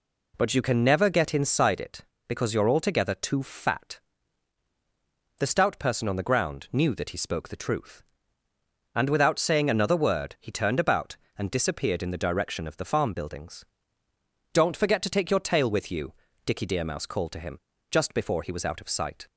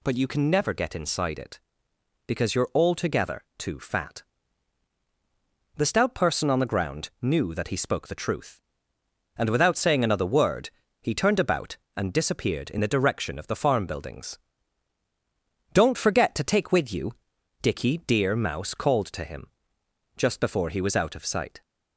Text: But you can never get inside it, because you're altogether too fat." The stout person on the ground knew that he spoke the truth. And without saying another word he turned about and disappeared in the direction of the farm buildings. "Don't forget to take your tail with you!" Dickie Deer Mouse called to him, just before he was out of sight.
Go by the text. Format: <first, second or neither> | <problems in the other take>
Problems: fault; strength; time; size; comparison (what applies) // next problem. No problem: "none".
first | pauses between "word" and "he"; slight; at 10.6 s; 0.32 s long // skips "your tail"; at 16.7 s